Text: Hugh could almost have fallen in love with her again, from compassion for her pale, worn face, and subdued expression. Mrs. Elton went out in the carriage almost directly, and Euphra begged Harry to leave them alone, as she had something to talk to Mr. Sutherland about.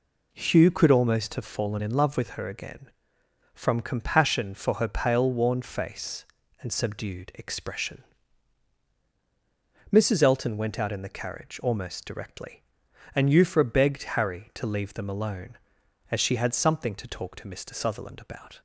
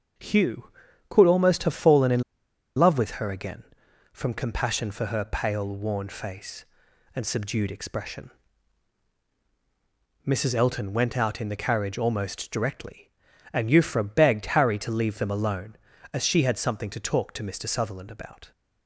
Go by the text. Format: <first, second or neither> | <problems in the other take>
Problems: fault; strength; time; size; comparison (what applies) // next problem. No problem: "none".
first | starts louder than the rest; until 1.5 s; 6.5 dB // pauses between "in" and "love"; noticeable; at 2.2 s; 0.56 s long